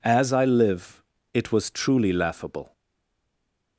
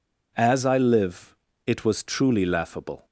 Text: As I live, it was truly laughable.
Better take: second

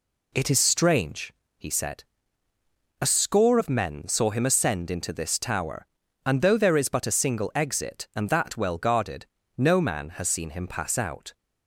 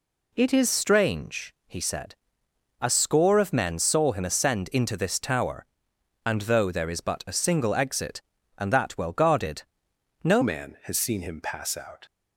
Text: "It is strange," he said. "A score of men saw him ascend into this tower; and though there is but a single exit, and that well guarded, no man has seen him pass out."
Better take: first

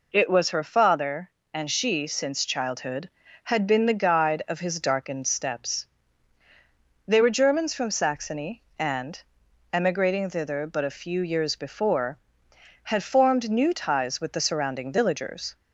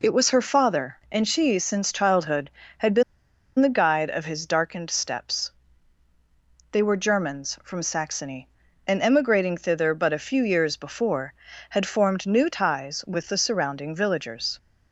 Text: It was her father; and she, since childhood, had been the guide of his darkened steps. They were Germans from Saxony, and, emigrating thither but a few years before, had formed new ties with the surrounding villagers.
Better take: first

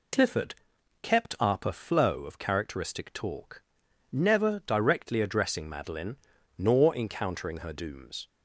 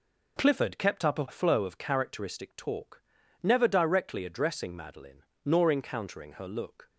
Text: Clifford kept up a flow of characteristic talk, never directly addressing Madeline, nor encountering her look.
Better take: second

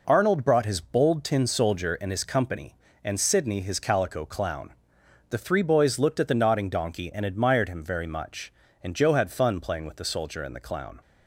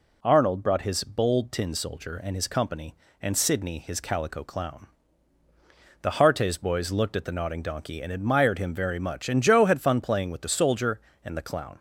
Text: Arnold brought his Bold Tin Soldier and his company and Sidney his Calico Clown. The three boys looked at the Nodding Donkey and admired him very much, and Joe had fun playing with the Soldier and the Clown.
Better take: first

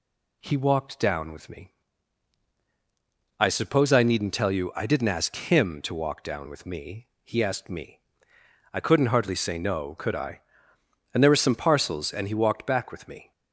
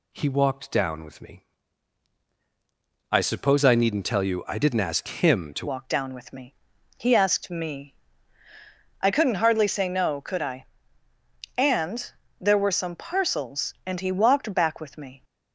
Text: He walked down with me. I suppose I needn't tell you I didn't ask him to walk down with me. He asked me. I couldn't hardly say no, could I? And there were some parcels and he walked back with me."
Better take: first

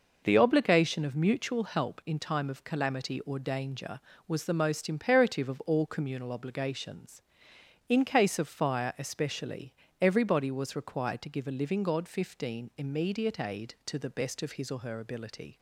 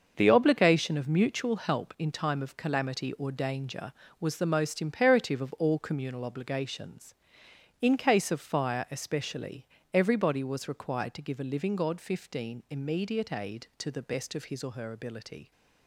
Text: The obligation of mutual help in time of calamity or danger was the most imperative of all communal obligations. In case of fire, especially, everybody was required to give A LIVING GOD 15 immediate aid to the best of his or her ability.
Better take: first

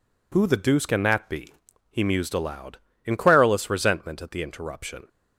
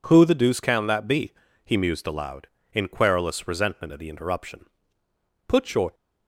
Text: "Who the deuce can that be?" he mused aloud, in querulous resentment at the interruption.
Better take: first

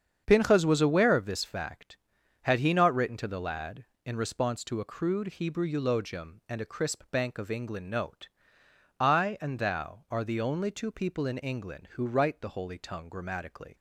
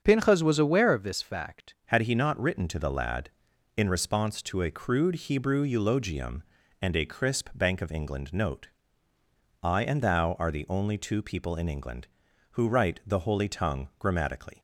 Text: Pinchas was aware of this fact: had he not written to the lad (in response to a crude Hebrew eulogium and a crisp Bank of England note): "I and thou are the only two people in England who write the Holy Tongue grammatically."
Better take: first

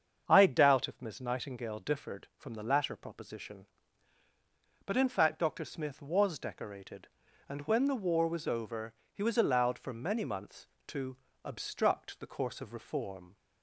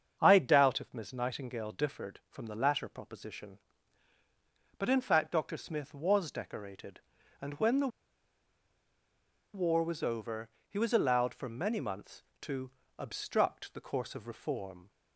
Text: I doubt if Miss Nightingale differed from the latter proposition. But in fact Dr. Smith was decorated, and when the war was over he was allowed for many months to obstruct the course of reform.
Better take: first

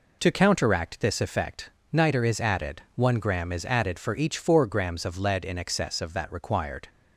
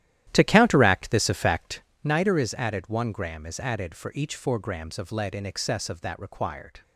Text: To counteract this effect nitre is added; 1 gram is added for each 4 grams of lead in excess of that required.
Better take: first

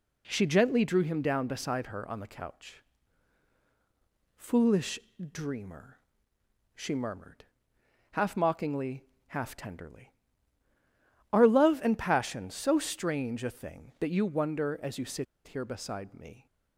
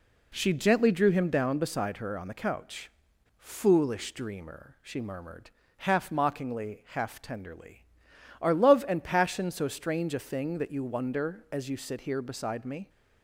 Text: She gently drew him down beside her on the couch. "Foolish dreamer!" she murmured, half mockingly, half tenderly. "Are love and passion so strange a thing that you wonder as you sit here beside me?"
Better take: second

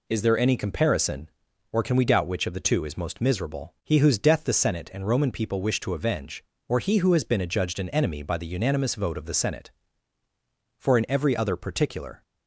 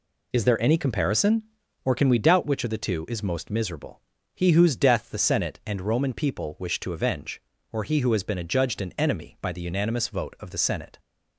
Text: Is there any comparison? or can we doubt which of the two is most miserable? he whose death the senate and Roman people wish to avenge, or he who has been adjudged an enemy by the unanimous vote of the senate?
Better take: second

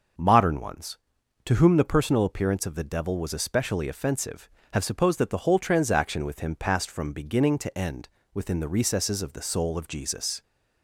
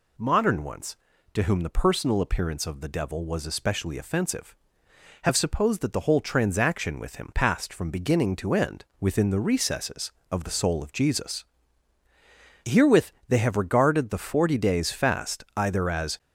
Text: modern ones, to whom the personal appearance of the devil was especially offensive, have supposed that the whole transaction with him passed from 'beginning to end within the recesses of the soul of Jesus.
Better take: first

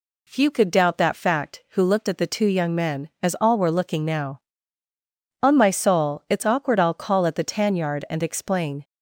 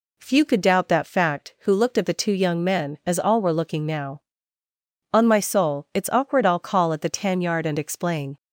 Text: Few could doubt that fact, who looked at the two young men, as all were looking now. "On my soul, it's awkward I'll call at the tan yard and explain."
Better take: neither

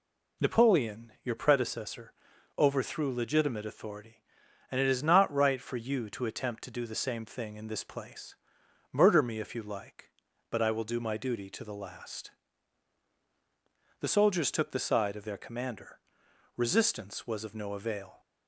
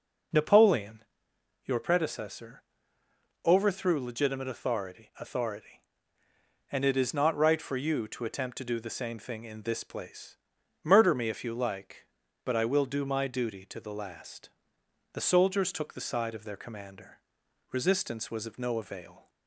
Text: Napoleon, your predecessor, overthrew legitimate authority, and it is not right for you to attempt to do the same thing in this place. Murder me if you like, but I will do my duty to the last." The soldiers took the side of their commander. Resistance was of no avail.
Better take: first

